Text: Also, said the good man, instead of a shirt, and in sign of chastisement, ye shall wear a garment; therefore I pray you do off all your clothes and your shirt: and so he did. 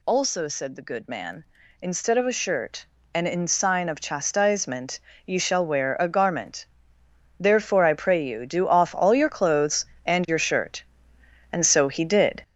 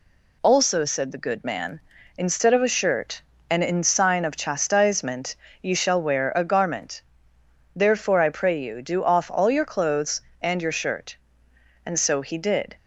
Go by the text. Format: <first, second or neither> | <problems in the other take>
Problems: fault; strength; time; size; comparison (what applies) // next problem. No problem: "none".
second | gets louder; noticeable; throughout; 6 dB